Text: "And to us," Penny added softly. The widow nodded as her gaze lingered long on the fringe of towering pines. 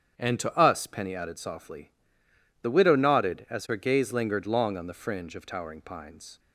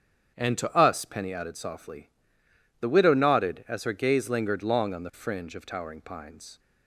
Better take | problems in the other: neither | starts louder than the rest; strong; the same in both

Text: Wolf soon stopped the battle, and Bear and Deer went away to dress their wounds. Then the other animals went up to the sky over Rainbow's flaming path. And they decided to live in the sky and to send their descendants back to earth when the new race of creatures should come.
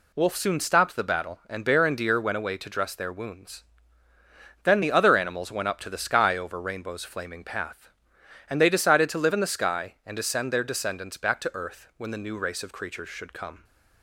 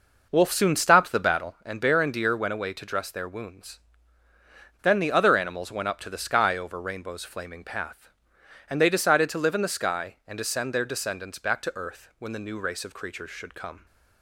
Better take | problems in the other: first | starts louder than the rest; noticeable; until 1.6 s; 5.5 dB

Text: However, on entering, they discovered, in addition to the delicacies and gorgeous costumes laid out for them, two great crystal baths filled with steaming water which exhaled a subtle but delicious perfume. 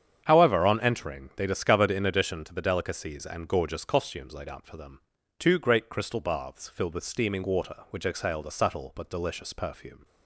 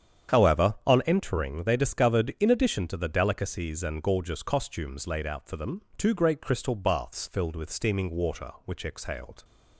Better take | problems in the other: first | starts louder than the rest; strong; until 1.4 s; 8.5 dB; strong in the first // stops before "a subtle but delicious perfume"; at 9.4 s

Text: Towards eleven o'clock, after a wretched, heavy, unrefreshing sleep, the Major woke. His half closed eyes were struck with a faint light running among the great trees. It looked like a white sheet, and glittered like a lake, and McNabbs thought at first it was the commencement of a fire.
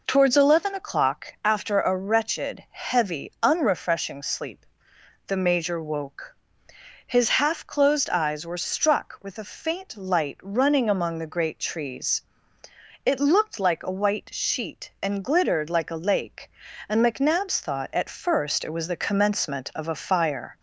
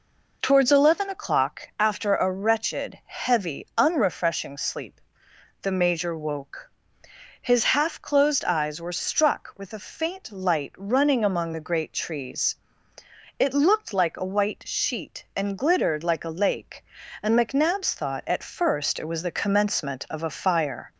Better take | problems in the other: neither | none

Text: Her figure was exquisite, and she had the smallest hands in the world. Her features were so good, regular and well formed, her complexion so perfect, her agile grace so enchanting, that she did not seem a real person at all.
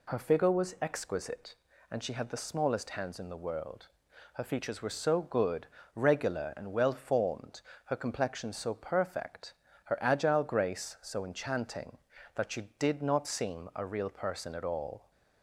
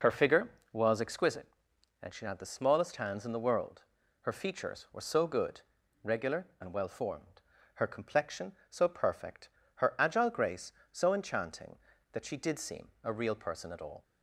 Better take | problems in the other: first | skips "not"; at 12.5 s // pauses between "seem" and "a"; slight; at 12.8 s; 0.16 s long

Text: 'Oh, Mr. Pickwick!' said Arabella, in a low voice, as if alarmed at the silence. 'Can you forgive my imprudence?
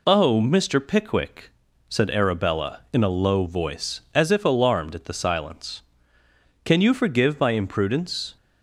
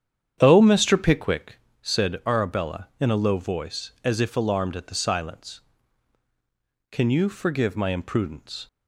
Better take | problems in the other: first | starts louder than the rest; strong; until 1.5 s; 9 dB

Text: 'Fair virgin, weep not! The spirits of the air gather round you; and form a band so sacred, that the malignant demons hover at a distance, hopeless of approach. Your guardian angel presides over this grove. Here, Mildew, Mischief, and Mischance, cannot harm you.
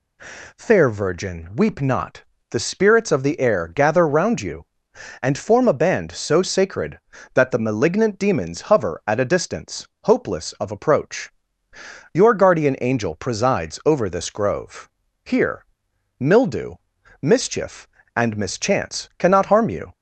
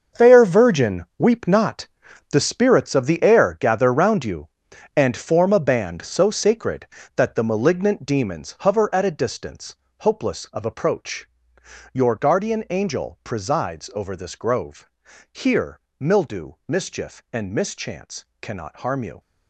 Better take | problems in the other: first | gets quieter; strong; throughout; 11 dB

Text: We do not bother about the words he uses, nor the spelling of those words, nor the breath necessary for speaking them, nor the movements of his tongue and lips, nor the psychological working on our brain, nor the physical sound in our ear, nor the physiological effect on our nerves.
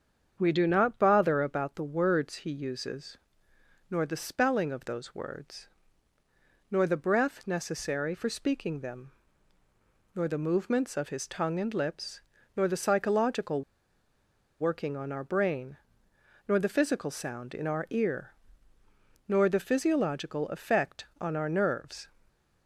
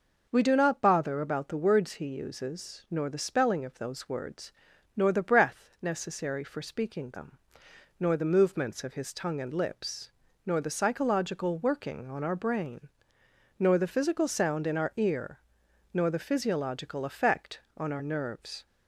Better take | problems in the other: second | starts louder than the rest; strong; until 1.3 s; 7.5 dB // pauses between "psychological" and "working"; at 13.6 s; 0.99 s long

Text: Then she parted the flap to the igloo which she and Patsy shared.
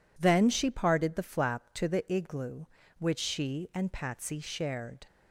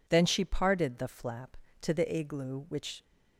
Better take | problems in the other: first | stops before "she and Patsy shared"; at 3.0 s

